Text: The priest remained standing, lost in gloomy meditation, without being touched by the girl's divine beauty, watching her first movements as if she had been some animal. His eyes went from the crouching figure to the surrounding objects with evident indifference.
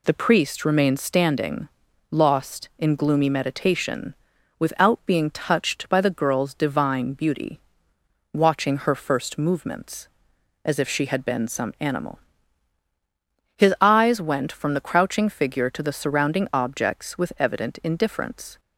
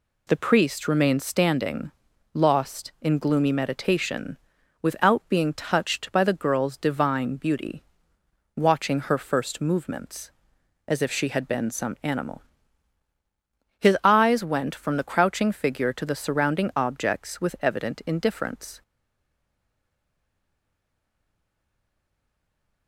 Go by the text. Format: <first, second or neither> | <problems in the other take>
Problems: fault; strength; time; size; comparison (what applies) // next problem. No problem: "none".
first | stays silent after the last word; strong; from 18.8 s on; 4.0 s long